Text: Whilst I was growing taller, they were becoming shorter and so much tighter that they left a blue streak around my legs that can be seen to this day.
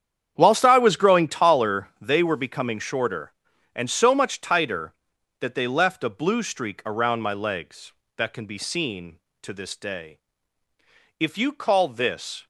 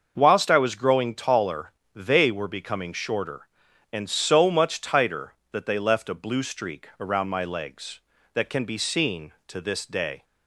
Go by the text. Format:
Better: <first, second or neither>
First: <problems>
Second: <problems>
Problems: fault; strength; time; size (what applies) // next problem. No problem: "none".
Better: second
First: starts louder than the rest; strong; until 1.3 s; 8.5 dB // goes on to say "If you call this"; noticeable; from 11.1 s on; 1.2 s long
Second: starts louder than the rest; until 1.1 s; 6.5 dB